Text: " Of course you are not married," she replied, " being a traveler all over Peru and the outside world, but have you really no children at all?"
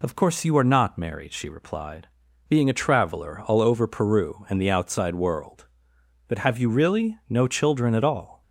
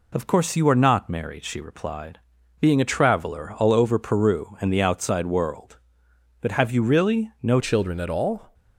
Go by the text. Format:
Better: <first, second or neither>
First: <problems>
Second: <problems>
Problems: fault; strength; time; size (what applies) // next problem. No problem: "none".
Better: first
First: none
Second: changes voice at "children"; from 7.6 s on; 0.9 s long